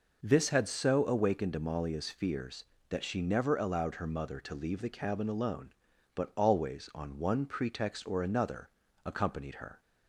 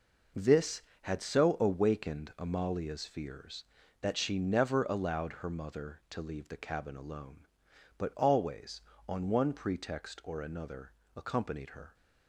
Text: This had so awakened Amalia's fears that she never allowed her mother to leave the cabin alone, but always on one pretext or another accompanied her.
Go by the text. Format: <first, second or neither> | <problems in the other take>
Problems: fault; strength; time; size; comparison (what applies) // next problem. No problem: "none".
neither | pauses between "another" and "accompanied"; slight; the same in both